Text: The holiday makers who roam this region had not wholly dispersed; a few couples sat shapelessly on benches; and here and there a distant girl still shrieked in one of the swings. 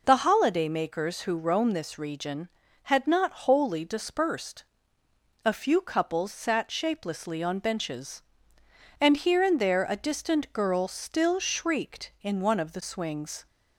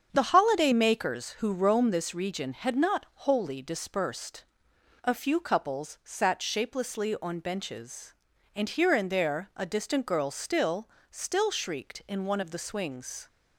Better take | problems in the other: first | starts louder than the rest; strong; until 1.1 s; 7 dB // says "still" twice; at 11.1 s

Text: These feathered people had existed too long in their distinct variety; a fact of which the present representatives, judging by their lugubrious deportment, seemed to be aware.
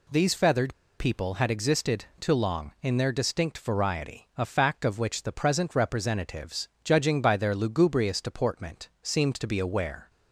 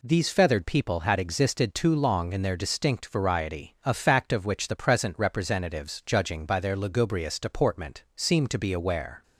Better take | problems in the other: second | pauses between "feathered" and "people"; slight; at 0.7 s; 0.24 s long

